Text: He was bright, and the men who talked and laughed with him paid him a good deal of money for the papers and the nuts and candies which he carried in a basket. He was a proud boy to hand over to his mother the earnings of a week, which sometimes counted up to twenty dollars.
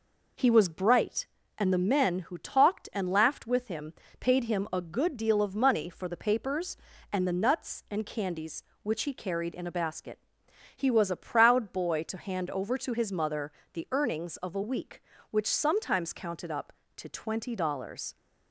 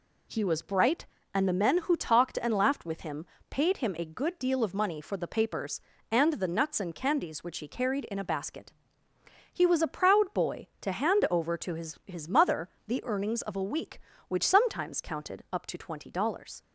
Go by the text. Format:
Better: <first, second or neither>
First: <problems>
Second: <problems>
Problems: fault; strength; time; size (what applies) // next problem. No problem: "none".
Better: first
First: pauses between "him" and "paid"; slight; at 3.9 s; 0.26 s long // pauses between "mother" and "the"; slight; at 13.5 s; 0.22 s long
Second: pauses between "him" and "paid"; slight; at 3.2 s; 0.24 s long // says "his" twice; at 12.0 s // pauses between "mother" and "the"; slight; at 12.6 s; 0.16 s long